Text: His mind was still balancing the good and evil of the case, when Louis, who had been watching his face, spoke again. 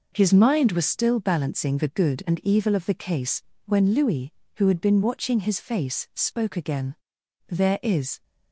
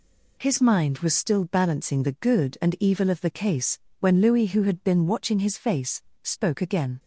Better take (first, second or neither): second